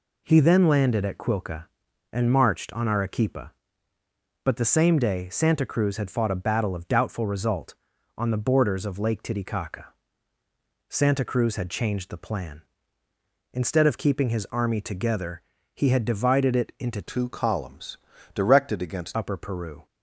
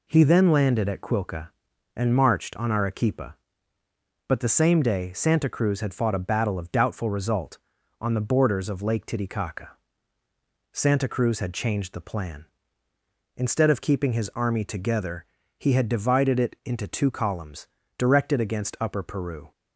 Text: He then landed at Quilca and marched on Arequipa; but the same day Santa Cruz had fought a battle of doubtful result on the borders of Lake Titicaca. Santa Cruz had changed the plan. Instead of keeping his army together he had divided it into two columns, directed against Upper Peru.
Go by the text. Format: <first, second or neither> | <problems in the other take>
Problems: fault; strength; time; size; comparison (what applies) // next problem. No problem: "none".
second | pauses between "together" and "he"; slight; at 15.4 s; 0.34 s long; slight in the second // changes voice from "two" to "against"; from 17.0 to 19.1 s; 2.1 s long